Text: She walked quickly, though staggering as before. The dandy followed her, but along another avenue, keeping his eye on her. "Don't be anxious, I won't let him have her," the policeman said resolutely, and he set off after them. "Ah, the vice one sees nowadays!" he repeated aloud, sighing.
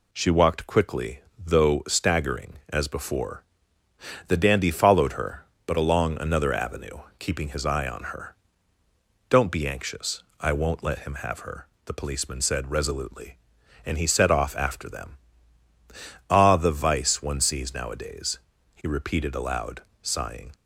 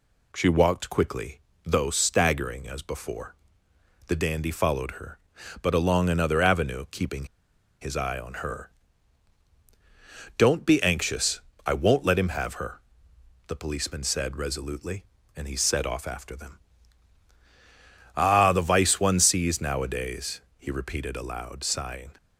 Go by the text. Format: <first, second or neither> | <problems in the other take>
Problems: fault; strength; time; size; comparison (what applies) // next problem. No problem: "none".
first | pauses between "keeping" and "his"; noticeable; at 7.2 s; 0.56 s long